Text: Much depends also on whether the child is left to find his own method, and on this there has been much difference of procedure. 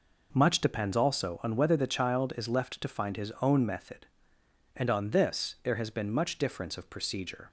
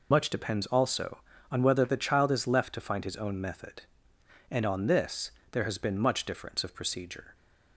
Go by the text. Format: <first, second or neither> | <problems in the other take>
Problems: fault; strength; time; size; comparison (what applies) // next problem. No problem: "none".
first | loses the start of "Much"; at 0.1 s; 85 ms // pauses between "this" and "there"; slight; at 5.3 s; 0.20 s long